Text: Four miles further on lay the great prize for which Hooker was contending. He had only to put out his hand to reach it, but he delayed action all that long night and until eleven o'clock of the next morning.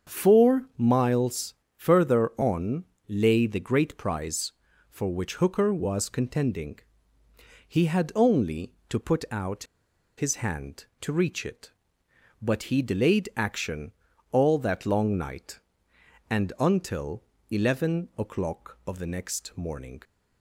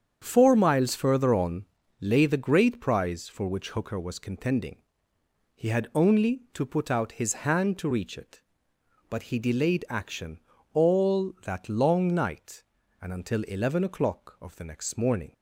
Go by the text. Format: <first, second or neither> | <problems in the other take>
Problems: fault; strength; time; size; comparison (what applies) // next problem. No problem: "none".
second | starts louder than the rest; strong; until 1.2 s; 7 dB; strong in the second // pauses between "miles" and "further"; slight; at 1.5 s; 0.24 s long // pauses between "on" and "lay"; slight; at 2.8 s; 0.24 s long; slight in the second // pauses between "out" and "his"; noticeable; at 9.6 s; 0.53 s long // pauses between "action" and "all"; at 13.9 s; 0.38 s long; also in the second // pauses between "until" and "eleven"; slight; at 17.2 s; 0.26 s long